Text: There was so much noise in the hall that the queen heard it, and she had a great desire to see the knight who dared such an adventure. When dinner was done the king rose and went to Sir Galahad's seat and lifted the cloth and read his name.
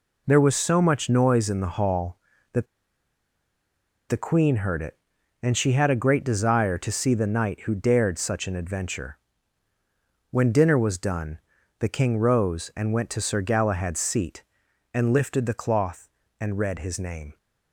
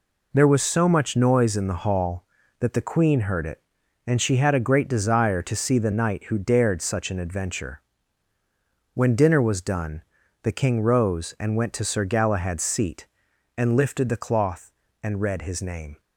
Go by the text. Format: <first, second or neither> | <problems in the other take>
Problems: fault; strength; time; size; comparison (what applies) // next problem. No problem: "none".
second | pauses between "that" and "the"; strong; at 2.6 s; 1.4 s long // pauses between "done" and "the"; at 11.3 s; 0.40 s long; also in the second